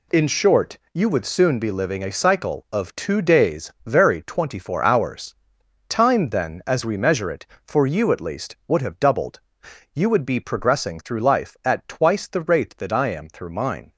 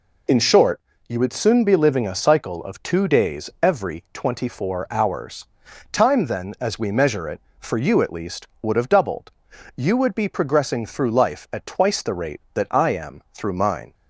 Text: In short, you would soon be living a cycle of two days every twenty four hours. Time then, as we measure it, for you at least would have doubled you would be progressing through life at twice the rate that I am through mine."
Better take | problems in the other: second | says "very" for "every"; at 3.8 s // pauses between "doubled" and "you"; noticeable; at 9.4 s; 0.53 s long; noticeable in the second

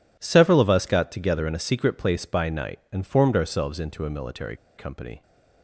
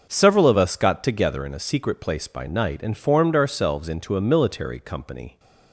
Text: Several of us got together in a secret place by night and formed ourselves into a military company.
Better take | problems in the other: second | pauses between "military" and "company"; slight; at 4.5 s; 0.20 s long

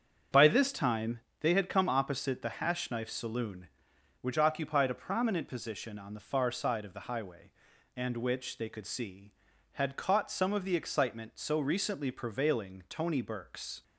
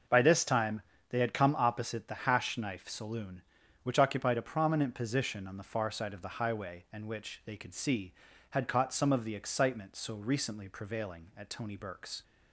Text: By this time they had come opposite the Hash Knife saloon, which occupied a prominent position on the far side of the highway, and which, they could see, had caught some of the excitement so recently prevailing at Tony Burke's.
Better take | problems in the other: second | starts louder than the rest; strong; until 1.5 s; 7.5 dB // pauses between "time" and "they"; slight; at 1.1 s; 0.22 s long; slight in the second // skips "at"; at 12.8 s

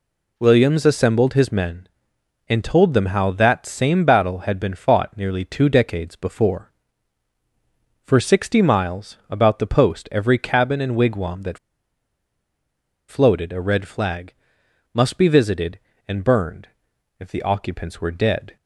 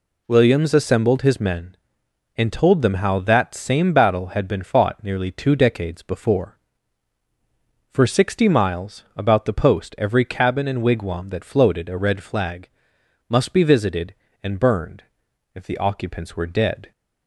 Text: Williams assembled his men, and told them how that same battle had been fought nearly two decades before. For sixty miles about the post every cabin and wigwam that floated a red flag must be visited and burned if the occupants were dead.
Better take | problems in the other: second | pauses between "that" and "floated"; strong; at 11.5 s; 1.5 s long // pauses between "flag" and "must"; noticeable; at 14.3 s; 0.60 s long; noticeable in the second // pauses between "burned" and "if"; noticeable; at 16.6 s; 0.54 s long; noticeable in the second

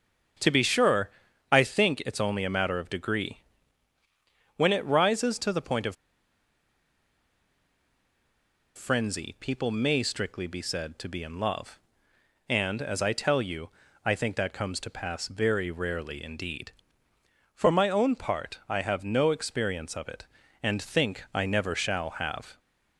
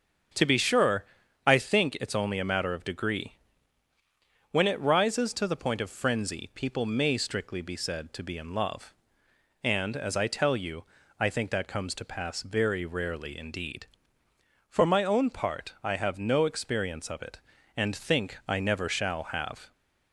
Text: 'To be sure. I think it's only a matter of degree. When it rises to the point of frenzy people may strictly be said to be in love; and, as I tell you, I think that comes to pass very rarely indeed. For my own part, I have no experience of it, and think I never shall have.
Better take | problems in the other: second | starts louder than the rest; until 1.7 s; 6.5 dB; also in the second // pauses between "of" and "frenzy"; strong; at 5.9 s; 2.8 s long

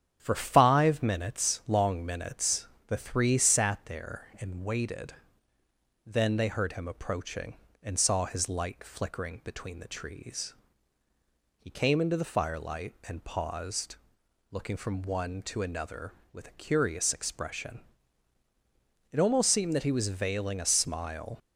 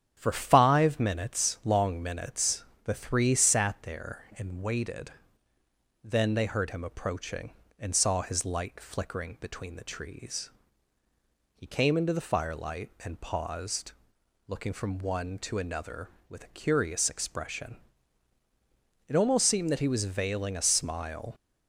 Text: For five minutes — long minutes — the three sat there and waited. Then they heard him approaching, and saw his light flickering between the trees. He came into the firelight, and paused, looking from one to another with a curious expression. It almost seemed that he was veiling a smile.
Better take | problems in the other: neither | starts louder than the rest; strong; the same in both

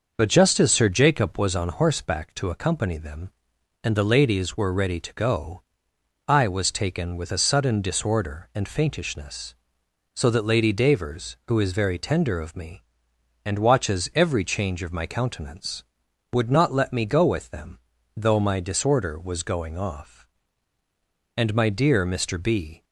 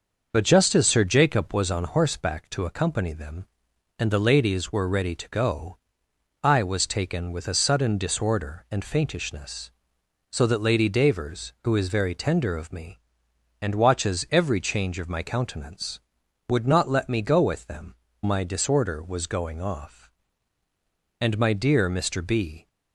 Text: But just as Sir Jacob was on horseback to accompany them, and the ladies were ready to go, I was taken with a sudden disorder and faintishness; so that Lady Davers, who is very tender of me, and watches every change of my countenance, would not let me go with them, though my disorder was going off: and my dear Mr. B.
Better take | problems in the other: first | starts louder than the rest; noticeable; until 1.3 s; 6 dB; noticeable in the first // skips "though"; at 18.0 s

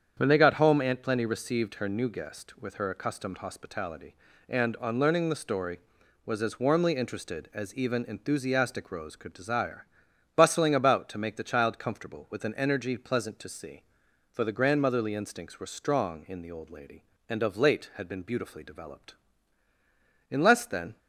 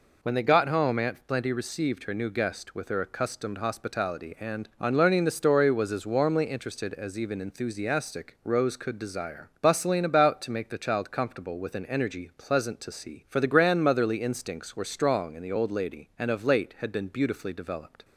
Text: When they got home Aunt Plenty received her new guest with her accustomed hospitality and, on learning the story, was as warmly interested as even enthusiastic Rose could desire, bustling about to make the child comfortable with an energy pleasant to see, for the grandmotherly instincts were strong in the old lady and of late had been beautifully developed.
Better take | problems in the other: second | starts louder than the rest; strong; until 1.1 s; 8 dB // goes on to say "In less than"; noticeable; from 20.2 s on; 0.68 s long

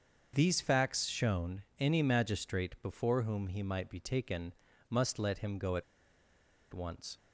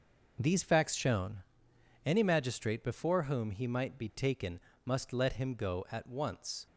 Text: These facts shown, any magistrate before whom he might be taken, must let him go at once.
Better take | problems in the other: second | starts louder than the rest; until 1.3 s; 6.5 dB // pauses between "at" and "once"; noticeable; at 5.8 s; 0.90 s long

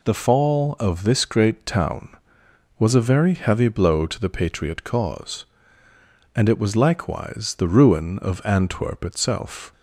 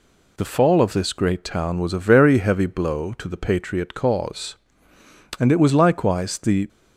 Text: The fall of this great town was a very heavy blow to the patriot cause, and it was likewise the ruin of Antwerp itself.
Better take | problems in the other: first | stops before "ruin of Antwerp itself"; at 6.6 s

